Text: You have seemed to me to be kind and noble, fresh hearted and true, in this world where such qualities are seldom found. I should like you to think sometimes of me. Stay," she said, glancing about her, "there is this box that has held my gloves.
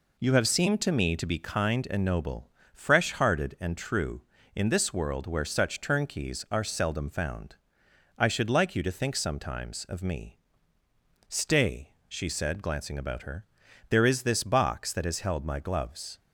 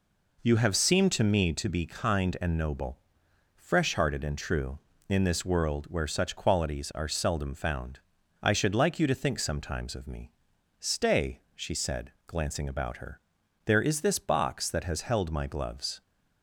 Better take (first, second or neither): second